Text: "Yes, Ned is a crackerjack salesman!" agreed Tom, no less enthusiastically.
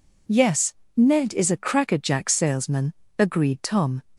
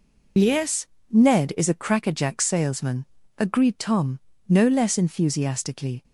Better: second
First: stops before "no less enthusiastically"; at 4.1 s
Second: none

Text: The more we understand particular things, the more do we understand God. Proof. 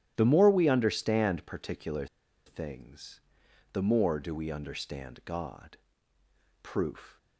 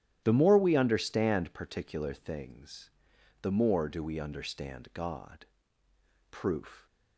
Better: second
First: starts louder than the rest; strong; until 1.1 s; 12 dB // pauses between "particular" and "things"; at 2.0 s; 0.40 s long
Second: starts louder than the rest; strong; until 1.2 s; 11.5 dB

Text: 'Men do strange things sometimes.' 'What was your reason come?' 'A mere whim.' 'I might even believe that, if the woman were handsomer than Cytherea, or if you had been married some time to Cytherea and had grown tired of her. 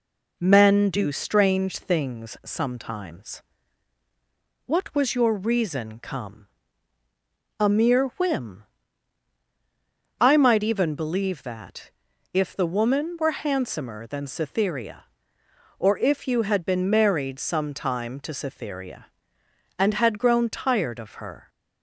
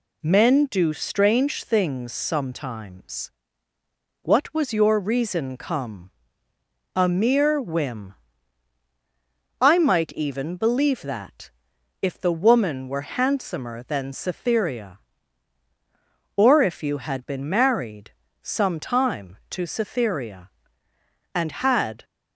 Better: first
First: none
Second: pauses between "married" and "some"; slight; at 18.1 s; 0.30 s long // stops before "grown tired of her"; at 22.0 s

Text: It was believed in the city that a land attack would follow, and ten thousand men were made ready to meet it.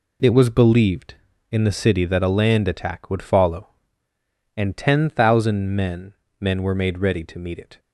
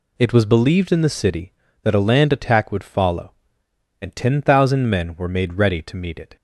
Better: second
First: says "men" twice; at 6.3 s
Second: none

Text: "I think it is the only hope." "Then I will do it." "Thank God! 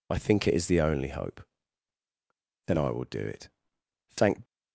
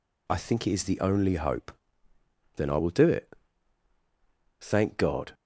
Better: second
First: stops before "God"; at 4.4 s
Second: none

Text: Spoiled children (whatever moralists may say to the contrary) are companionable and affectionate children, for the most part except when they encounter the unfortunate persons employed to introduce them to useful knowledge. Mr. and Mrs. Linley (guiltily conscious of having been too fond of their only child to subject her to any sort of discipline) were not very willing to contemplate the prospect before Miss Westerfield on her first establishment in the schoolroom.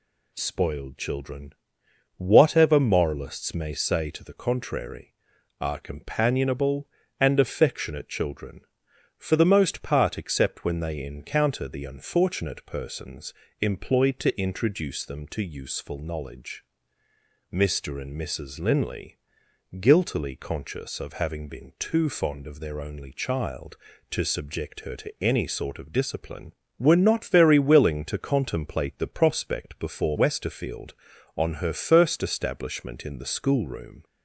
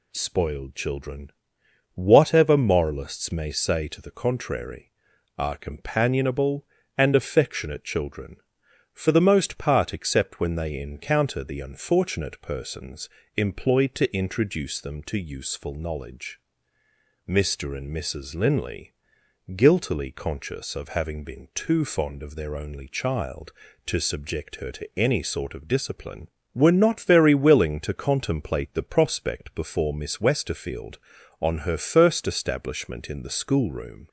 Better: second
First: pauses between "persons" and "employed"; slight; at 13.3 s; 0.28 s long // skips "Miss"; at 30.1 s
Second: pauses between "persons" and "employed"; slight; at 13.0 s; 0.28 s long

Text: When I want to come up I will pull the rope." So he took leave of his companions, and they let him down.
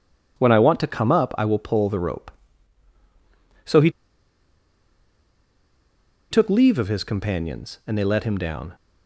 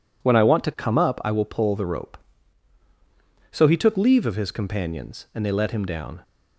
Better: second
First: pauses between "he" and "took"; strong; at 3.8 s; 2.4 s long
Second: none

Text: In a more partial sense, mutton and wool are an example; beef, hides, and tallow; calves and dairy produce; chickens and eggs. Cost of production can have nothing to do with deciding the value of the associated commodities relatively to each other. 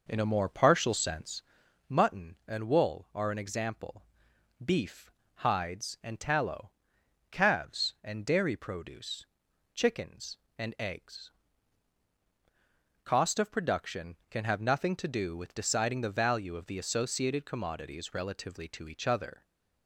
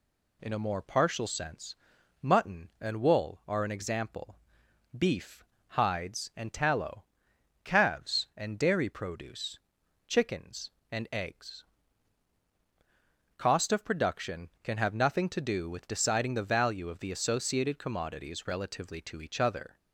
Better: second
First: starts louder than the rest; noticeable; until 1.6 s; 5.5 dB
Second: none

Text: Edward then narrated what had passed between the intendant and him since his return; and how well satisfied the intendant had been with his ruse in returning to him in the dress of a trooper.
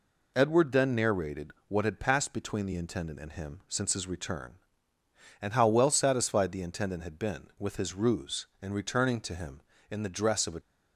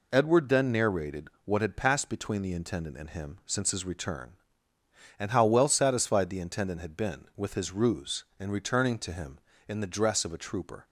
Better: second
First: pauses between "narrated" and "what"; slight; at 1.4 s; 0.18 s long // stops before "trooper"; at 10.6 s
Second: pauses between "narrated" and "what"; slight; at 1.2 s; 0.18 s long

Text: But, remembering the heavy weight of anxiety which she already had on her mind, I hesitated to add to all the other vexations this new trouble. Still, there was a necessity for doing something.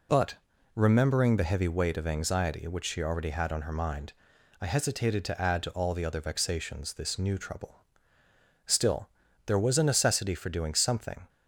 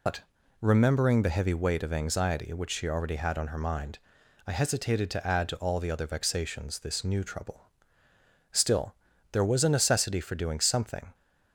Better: first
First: none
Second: loses the start of "But"; at 0.0 s; 110 ms

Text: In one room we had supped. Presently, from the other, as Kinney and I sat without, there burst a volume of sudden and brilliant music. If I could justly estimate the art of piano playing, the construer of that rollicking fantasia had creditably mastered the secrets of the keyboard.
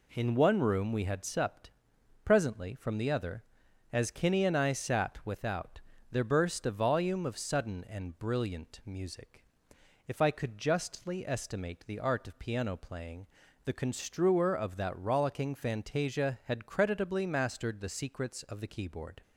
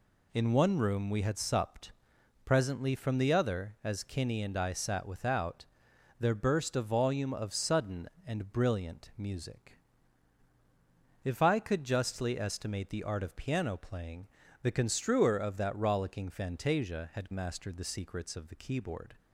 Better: first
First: none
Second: skips "creditably"; at 17.3 s

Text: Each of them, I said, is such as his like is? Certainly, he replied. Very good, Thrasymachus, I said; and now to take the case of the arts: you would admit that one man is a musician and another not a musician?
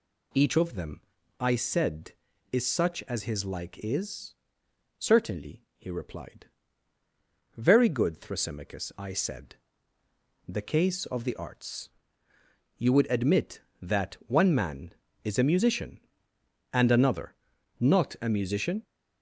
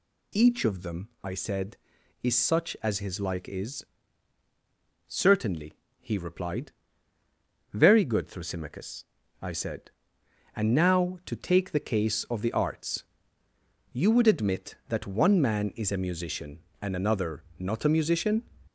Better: second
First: skips "and now to take"; at 10.0 s // pauses between "another" and "not"; at 17.3 s; 0.42 s long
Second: pauses between "another" and "not"; slight; at 17.4 s; 0.16 s long

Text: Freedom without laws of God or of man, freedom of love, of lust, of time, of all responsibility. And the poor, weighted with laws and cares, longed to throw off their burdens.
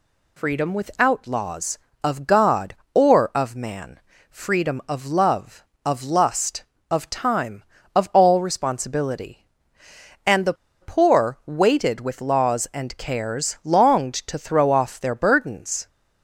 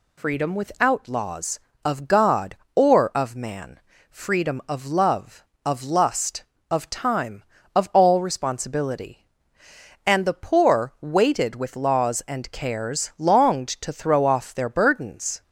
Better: second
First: pauses between "the" and "poor"; slight; at 10.5 s; 0.27 s long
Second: none

